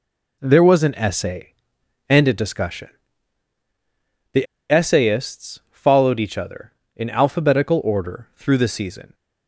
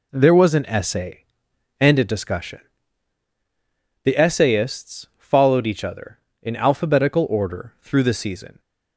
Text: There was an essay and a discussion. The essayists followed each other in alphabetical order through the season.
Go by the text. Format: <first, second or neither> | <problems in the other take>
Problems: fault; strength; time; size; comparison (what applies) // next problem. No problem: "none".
second | pauses between "The" and "essayists"; slight; at 4.4 s; 0.24 s long